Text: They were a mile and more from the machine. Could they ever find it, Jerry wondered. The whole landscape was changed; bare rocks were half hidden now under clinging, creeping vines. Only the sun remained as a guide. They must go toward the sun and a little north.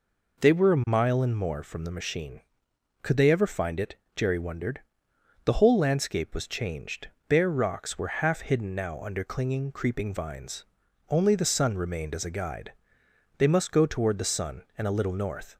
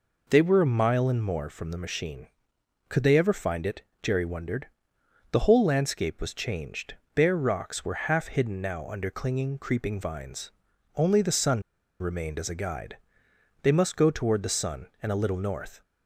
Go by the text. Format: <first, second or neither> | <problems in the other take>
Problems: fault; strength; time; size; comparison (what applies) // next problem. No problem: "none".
first | pauses between "sun" and "remained"; at 11.6 s; 0.38 s long